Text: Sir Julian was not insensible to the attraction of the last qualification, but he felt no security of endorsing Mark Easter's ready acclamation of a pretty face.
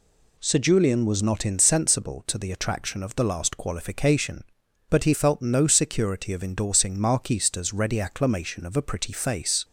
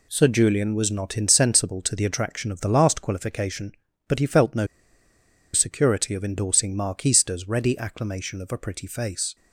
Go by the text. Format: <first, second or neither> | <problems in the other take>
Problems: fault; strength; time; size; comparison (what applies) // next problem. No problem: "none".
first | pauses between "no" and "security"; noticeable; at 4.6 s; 0.88 s long